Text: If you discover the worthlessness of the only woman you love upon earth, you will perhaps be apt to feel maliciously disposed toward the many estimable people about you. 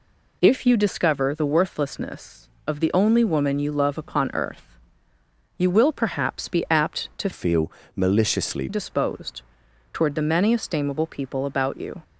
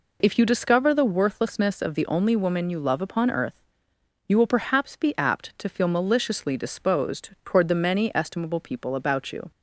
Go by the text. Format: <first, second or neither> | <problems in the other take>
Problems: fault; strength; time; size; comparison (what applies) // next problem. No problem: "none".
second | changes voice from "feel" to "maliciously"; from 7.3 to 8.6 s; 1.3 s long // pauses between "feel" and "maliciously"; slight; at 7.7 s; 0.24 s long // pauses between "disposed" and "toward"; noticeable; at 9.4 s; 0.50 s long